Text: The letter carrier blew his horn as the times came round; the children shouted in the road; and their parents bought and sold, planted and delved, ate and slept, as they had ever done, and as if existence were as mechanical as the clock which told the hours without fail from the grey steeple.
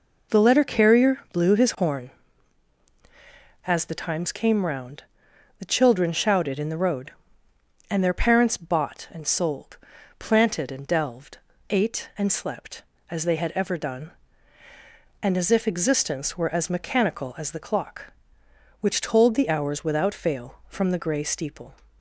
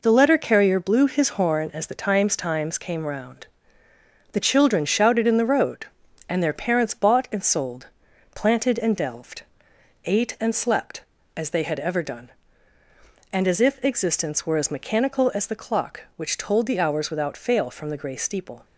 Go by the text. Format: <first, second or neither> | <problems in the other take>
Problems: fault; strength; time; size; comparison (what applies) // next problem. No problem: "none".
first | says "times" twice; at 2.3 s